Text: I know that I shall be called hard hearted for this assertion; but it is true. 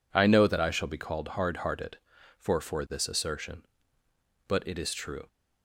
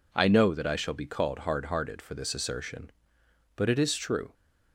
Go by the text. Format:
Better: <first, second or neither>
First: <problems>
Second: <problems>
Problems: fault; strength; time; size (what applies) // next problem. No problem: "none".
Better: second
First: says "for" twice; at 2.6 s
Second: none